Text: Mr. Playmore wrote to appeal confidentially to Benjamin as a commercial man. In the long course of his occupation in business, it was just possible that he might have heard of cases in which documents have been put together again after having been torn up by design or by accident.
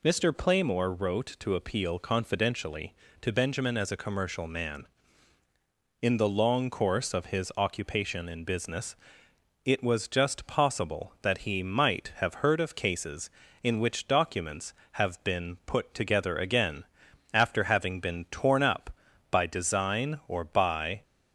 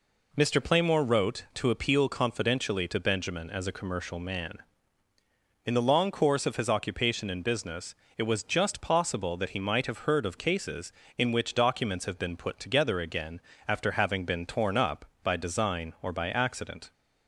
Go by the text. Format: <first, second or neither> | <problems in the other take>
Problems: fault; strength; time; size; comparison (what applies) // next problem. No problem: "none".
second | pauses between "again" and "after"; noticeable; at 16.8 s; 0.48 s long; slight in the second // stops before "accident"; at 21.0 s